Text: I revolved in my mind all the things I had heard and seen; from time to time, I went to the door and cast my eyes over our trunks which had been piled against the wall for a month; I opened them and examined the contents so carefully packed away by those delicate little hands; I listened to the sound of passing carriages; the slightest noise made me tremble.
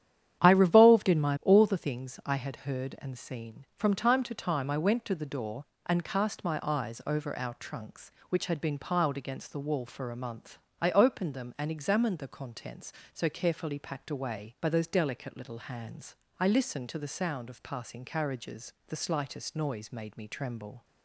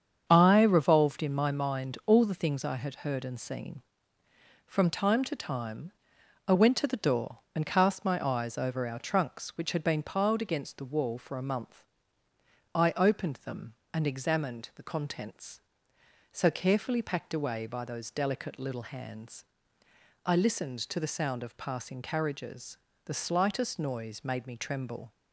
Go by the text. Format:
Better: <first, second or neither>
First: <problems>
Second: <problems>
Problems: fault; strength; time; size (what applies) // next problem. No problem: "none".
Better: second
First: starts louder than the rest; strong; until 1.4 s; 10 dB // skips "mind"; at 1.4 s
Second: starts louder than the rest; strong; until 1.2 s; 7.5 dB